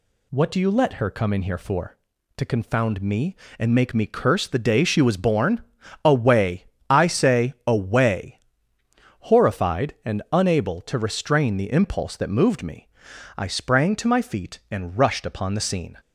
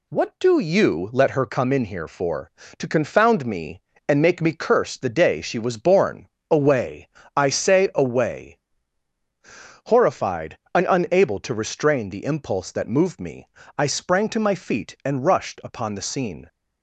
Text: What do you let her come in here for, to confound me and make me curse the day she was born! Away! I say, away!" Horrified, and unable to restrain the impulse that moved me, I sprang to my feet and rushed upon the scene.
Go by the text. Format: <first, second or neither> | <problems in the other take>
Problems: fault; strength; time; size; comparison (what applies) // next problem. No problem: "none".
neither | none